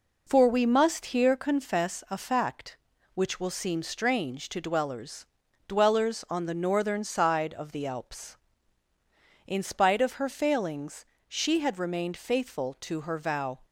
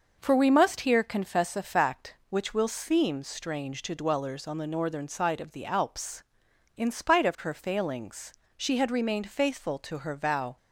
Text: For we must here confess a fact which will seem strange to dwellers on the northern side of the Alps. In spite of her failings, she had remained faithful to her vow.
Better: second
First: says "dwellers" twice; at 5.6 s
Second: none

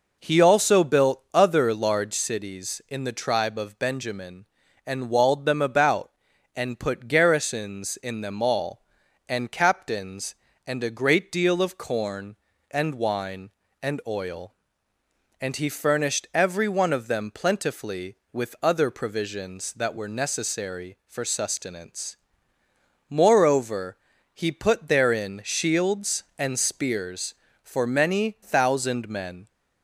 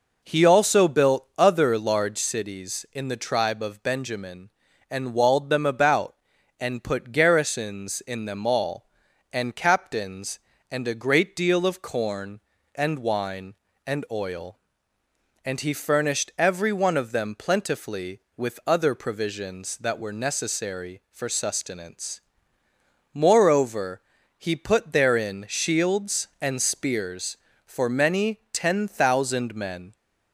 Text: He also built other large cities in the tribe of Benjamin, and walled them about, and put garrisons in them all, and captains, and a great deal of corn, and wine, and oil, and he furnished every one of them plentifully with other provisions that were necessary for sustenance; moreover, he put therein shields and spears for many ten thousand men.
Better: second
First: skips "ten"; at 28.3 s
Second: none

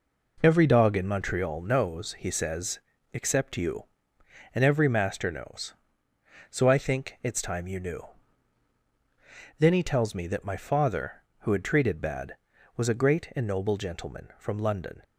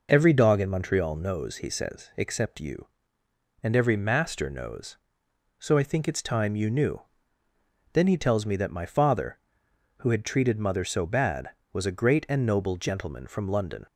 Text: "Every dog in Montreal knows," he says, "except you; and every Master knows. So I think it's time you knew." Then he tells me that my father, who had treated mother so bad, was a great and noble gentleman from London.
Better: second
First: skips "mother so"; at 12.0 s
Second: none

